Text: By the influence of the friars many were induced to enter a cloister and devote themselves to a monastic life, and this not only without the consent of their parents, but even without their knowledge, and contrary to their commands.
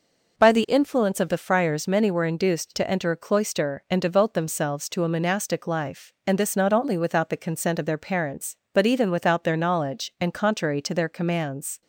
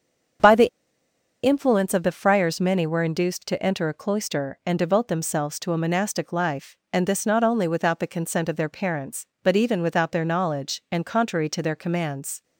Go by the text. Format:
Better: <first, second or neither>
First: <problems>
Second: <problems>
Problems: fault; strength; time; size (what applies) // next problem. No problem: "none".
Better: first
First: none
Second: starts louder than the rest; strong; until 2.1 s; 7 dB // pauses between "the" and "influence"; noticeable; at 0.6 s; 0.75 s long